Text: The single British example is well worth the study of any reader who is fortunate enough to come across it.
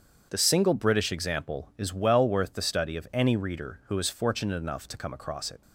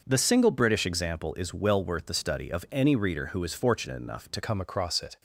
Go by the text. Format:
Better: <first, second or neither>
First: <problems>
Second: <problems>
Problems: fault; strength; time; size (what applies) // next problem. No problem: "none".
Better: first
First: starts louder than the rest; strong; until 1.3 s; 7.5 dB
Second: starts louder than the rest; until 1.0 s; 6 dB // changes voice at "come"; from 4.4 s on; 0.8 s long